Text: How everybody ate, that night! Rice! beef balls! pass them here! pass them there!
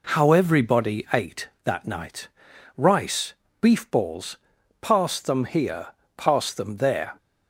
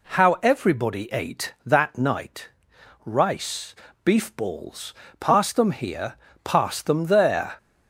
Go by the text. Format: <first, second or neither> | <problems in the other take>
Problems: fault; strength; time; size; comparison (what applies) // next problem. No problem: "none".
neither | none